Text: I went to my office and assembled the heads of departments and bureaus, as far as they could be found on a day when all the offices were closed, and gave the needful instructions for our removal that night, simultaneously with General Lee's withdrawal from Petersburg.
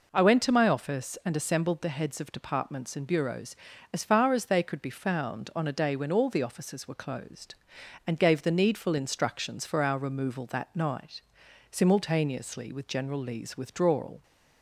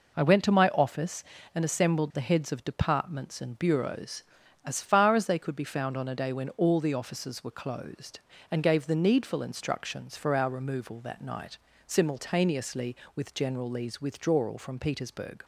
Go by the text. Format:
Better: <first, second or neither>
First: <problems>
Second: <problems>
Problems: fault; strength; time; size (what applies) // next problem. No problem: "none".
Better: second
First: stops before "from Petersburg"; at 14.2 s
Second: none